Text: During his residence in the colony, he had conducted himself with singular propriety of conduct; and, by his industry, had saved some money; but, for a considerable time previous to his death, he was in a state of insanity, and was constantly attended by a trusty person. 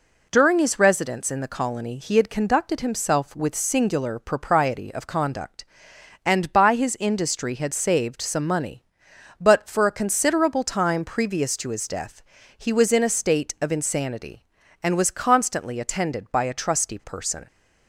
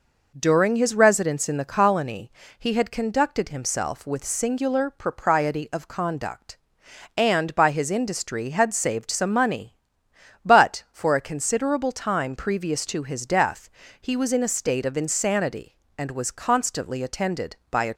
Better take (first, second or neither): first